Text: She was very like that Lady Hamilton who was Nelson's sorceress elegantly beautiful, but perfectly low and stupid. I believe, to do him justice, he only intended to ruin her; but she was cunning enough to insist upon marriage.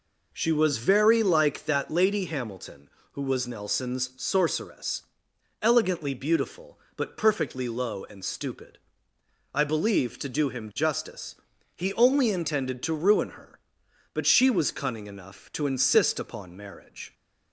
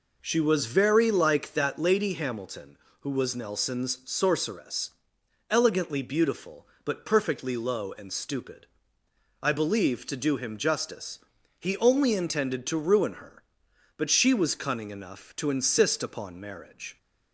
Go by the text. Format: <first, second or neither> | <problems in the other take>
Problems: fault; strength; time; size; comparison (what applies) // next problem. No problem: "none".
neither | pauses between "sorceress" and "elegantly"; noticeable; the same in both